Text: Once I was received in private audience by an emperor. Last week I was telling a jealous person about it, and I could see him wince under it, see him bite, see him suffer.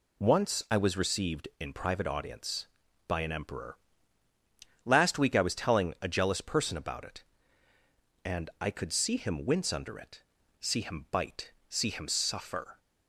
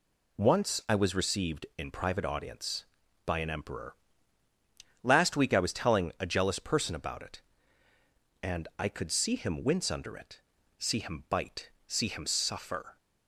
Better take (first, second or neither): neither